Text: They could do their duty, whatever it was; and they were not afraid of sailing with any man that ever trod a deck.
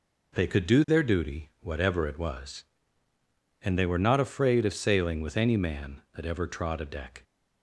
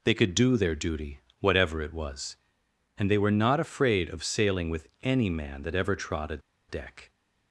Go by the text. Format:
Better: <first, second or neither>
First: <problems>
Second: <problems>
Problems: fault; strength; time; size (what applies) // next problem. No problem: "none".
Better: first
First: none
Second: pauses between "a" and "deck"; slight; at 6.3 s; 0.30 s long